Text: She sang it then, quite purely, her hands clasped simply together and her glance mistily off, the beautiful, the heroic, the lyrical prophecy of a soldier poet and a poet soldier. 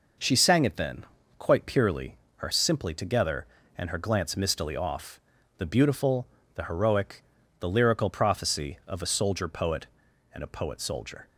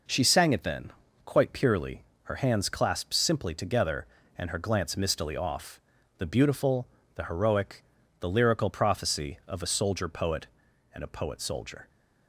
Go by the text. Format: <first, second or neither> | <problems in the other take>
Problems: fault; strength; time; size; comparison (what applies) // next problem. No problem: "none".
second | skips "hands clasped"; at 2.5 s